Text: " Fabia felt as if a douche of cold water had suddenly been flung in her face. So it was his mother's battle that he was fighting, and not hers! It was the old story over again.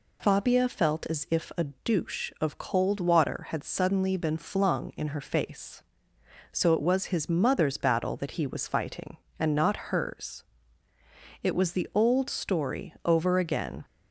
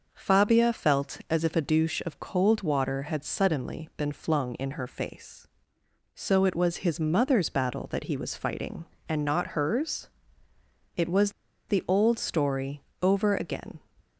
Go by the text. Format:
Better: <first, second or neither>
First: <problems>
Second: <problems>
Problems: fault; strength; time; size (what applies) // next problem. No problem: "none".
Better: first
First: none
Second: pauses between "was" and "the"; at 11.3 s; 0.37 s long // pauses between "story" and "over"; slight; at 12.8 s; 0.22 s long